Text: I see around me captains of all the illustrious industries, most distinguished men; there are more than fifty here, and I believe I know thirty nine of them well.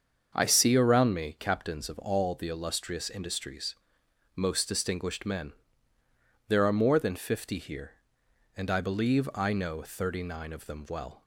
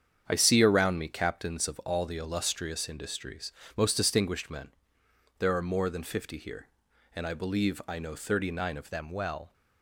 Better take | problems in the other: first | starts louder than the rest; strong; until 1.2 s; 8 dB; also in the first // changes voice at "them"; from 8.8 s on; 0.7 s long

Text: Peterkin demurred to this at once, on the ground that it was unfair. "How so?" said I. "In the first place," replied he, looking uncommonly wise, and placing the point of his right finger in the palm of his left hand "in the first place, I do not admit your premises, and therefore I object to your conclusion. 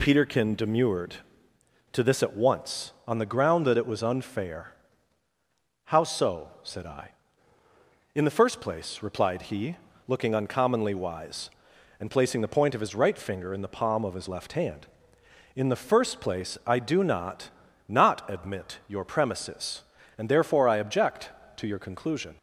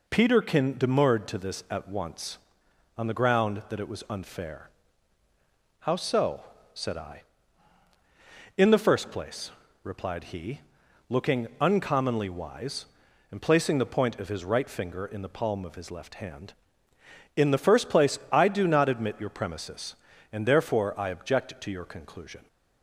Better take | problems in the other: second | says "not" twice; at 17.8 s

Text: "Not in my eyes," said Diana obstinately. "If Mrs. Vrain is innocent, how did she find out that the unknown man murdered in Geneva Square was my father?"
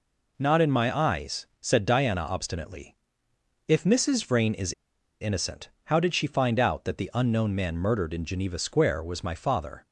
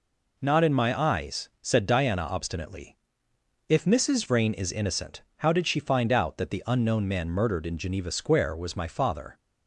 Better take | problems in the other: second | pauses between "is" and "innocent"; noticeable; at 4.7 s; 0.48 s long

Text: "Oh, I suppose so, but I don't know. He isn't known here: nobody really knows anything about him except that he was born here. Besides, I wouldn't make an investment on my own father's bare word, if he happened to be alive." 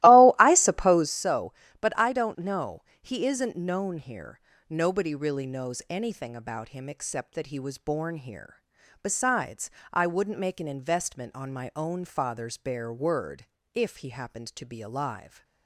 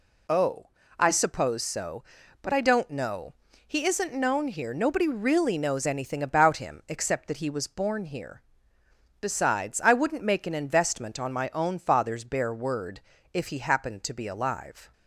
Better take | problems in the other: second | starts louder than the rest; strong; until 1.2 s; 16 dB

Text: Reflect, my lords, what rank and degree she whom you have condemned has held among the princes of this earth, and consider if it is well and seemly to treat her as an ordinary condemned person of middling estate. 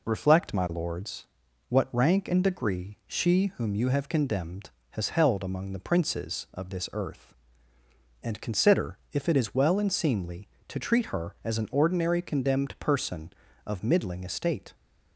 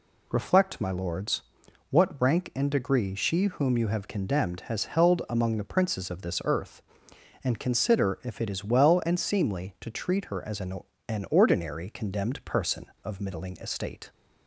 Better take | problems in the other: first | says "an" twice; at 11.1 s

